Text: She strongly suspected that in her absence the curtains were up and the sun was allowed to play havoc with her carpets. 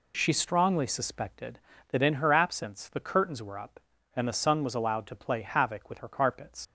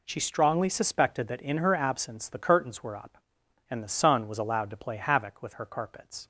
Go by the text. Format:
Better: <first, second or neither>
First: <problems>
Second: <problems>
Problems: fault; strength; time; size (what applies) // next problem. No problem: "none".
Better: second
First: leaves "carpets" unfinished; at 6.6 s; 115 ms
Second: none